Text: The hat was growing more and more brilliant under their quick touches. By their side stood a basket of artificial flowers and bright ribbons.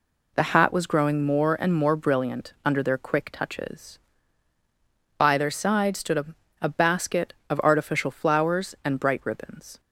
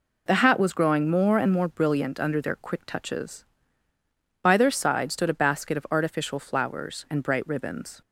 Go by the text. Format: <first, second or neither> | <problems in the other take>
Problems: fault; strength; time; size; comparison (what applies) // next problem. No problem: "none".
second | says "a" twice; at 6.6 s